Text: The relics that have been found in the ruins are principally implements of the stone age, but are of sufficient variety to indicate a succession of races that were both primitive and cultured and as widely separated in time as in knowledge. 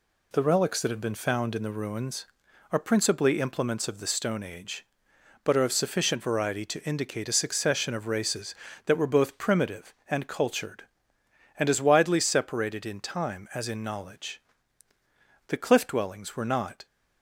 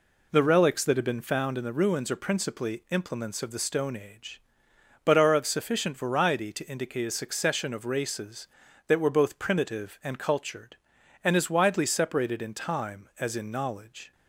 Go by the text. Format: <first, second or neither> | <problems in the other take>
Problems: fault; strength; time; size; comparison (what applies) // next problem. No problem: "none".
second | goes on to say "The cliff dwellings were not"; from 15.4 s on; 1.3 s long